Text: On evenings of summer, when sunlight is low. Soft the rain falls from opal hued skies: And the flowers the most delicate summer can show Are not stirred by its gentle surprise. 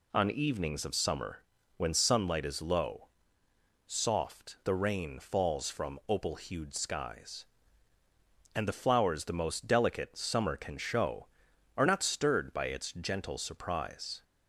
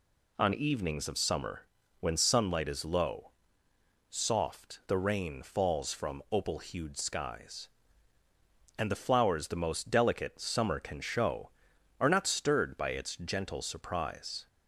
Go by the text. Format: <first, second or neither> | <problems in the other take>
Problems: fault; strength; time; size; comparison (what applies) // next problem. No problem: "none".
neither | none